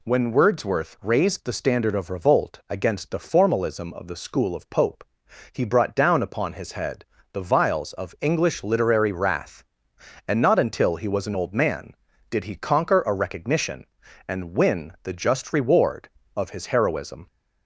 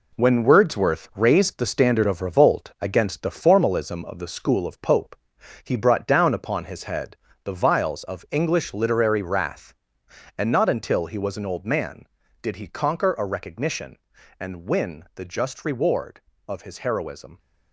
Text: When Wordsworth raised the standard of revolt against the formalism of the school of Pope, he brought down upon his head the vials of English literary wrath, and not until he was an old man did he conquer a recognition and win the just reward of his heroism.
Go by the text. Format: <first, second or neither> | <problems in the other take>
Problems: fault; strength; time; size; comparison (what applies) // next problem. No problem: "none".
first | gets quieter; strong; throughout; 7.5 dB // pauses between "head" and "the"; slight; at 7.1 s; 0.28 s long; slight in the first